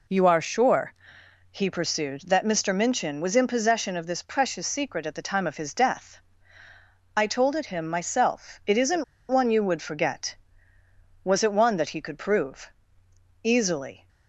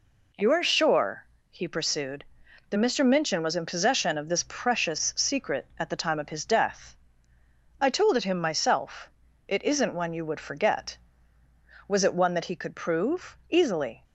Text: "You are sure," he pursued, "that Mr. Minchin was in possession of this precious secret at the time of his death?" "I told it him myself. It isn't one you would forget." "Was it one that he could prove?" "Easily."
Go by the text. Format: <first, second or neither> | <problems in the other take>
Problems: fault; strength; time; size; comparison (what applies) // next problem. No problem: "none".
second | pauses between "isn't" and "one"; slight; at 9.0 s; 0.25 s long